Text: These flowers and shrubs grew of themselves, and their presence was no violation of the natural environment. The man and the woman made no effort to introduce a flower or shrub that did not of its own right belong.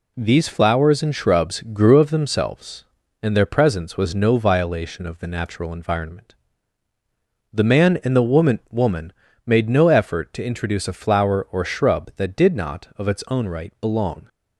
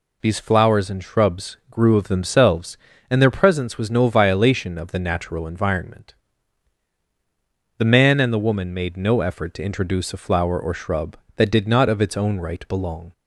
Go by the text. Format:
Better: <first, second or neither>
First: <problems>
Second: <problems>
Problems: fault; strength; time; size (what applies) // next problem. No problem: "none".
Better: second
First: says "woman" twice; at 8.6 s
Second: none